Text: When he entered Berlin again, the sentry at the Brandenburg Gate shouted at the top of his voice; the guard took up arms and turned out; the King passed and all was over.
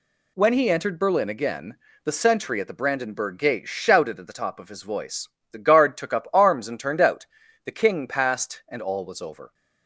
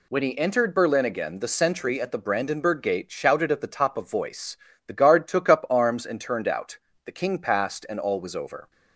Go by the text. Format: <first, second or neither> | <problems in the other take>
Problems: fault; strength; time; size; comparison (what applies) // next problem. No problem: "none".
first | skips "his"; at 4.0 s